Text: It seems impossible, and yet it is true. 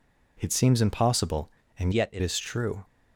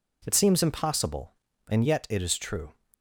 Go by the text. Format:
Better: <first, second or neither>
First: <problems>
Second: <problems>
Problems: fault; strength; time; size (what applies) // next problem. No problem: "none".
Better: second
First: changes voice from "yet" to "it"; from 1.9 to 2.2 s; 0.3 s long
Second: none